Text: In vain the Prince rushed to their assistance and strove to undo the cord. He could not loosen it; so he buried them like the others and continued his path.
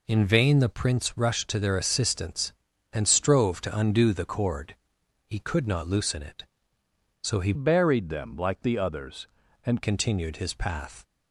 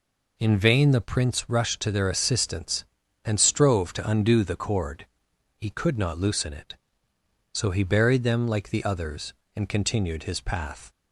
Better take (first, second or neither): second